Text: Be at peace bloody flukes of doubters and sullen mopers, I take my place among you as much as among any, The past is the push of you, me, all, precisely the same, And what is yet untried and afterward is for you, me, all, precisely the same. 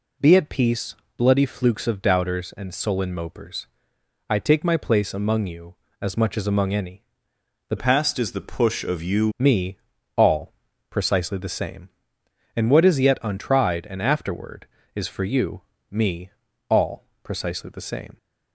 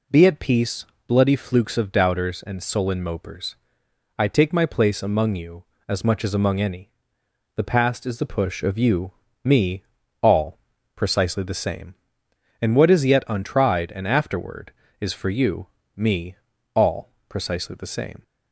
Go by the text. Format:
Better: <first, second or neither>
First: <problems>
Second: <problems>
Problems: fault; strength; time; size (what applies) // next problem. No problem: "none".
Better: second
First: pauses between "peace" and "bloody"; slight; at 0.9 s; 0.22 s long // changes voice from "past" to "you"; from 7.7 to 9.3 s; 1.6 s long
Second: pauses between "peace" and "bloody"; slight; at 0.8 s; 0.22 s long